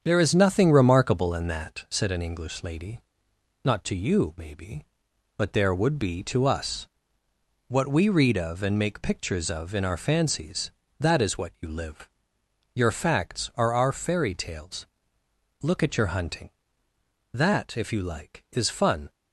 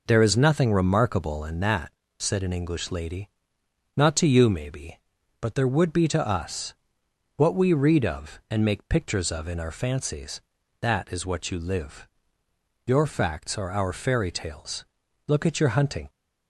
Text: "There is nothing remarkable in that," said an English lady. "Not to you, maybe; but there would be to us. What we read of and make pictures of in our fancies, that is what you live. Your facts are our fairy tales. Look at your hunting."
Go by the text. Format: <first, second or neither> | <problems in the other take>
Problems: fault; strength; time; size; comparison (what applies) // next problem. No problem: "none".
second | starts louder than the rest; strong; until 1.0 s; 7.5 dB // goes on to say "That if you like is fun"; strong; from 17.3 s on; 1.7 s long